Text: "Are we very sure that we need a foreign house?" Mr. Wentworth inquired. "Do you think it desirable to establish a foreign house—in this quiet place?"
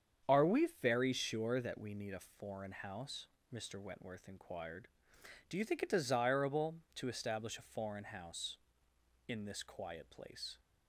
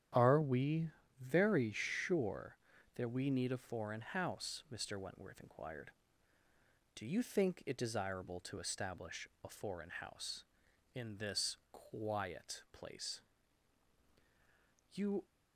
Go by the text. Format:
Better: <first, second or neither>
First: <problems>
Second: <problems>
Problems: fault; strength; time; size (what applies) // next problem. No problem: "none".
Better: first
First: starts louder than the rest; strong; until 1.4 s; 8 dB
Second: starts louder than the rest; strong; until 1.4 s; 10 dB // pauses between "we" and "very"; slight; at 0.9 s; 0.28 s long // pauses between "establish" and "a"; slight; at 9.2 s; 0.16 s long // goes on to say "You"; slight; from 14.9 s on; 0.32 s long